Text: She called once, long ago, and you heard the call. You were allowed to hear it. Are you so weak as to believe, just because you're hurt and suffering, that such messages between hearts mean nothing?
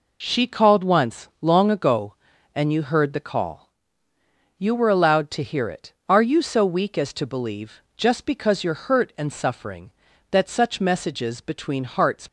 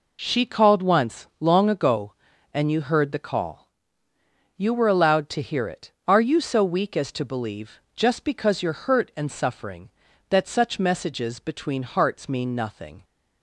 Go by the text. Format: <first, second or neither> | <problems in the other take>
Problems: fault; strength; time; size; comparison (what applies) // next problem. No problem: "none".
second | stops before "mean nothing"; at 12.2 s